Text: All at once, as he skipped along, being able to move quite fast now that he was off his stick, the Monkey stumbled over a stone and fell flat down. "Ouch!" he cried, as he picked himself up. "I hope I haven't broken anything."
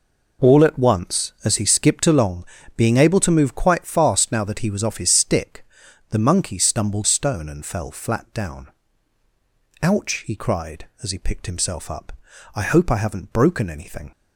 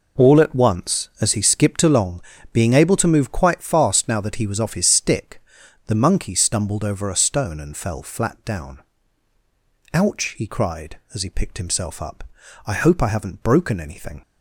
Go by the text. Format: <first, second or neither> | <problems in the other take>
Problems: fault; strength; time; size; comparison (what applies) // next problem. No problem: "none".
second | skips "over a"; at 7.0 s